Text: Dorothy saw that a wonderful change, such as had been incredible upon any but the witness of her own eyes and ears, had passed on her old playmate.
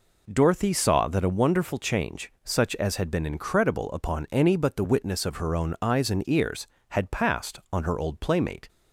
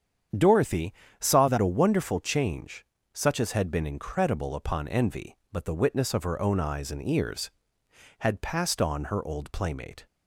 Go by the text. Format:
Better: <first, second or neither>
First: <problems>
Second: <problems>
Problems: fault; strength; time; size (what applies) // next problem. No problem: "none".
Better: first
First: none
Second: starts louder than the rest; strong; until 1.6 s; 8 dB // pauses between "Dorothy" and "saw"; slight; at 0.9 s; 0.26 s long // says "envy" for "any"; at 4.8 s